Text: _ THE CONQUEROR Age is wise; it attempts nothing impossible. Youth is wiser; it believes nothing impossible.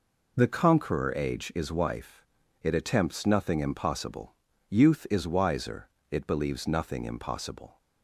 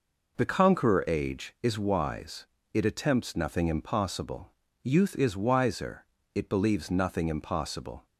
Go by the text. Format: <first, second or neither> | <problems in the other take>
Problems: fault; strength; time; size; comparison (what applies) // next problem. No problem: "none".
second | says "wife" for "wise"; at 1.6 s